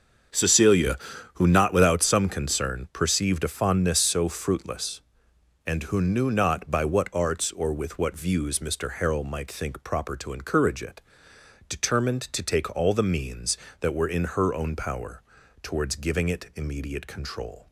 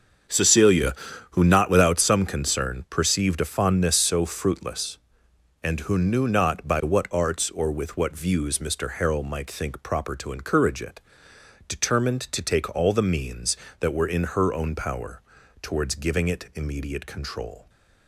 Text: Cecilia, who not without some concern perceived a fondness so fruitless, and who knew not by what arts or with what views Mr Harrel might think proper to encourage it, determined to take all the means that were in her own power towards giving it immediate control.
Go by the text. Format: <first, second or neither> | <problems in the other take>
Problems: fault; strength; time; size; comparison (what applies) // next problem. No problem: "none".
neither | starts louder than the rest; the same in both // pauses between "power" and "towards"; the same in both